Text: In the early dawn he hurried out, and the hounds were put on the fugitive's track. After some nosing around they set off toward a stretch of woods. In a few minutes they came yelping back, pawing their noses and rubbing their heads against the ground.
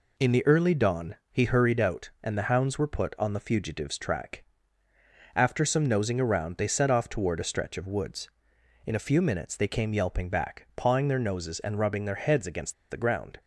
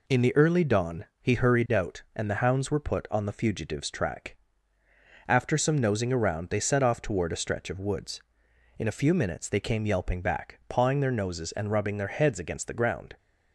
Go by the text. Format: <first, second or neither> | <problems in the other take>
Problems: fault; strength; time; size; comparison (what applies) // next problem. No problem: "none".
second | pauses between "against" and "the"; slight; at 12.7 s; 0.16 s long